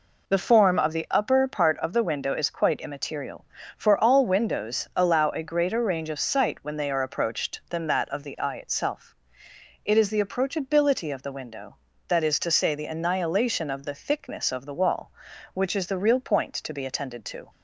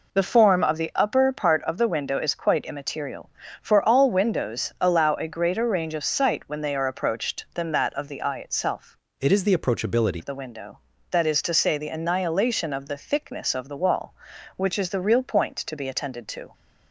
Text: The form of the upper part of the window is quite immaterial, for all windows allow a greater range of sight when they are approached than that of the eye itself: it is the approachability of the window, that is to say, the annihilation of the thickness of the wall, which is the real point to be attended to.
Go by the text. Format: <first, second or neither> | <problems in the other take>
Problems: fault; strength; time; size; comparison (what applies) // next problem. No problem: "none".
first | changes voice from "it" to "approachability"; from 9.1 to 10.2 s; 1.1 s long